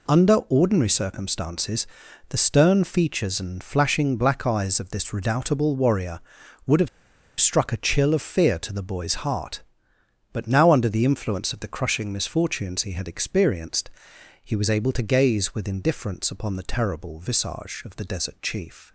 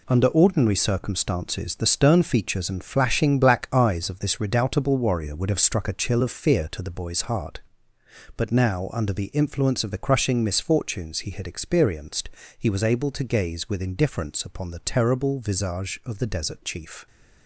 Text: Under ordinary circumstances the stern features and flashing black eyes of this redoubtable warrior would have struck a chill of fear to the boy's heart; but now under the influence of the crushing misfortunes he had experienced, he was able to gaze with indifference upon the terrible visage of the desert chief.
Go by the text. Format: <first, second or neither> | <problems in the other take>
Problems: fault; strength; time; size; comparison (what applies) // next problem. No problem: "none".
second | pauses between "circumstances" and "the"; at 1.8 s; 0.42 s long // pauses between "have" and "struck"; noticeable; at 6.8 s; 0.52 s long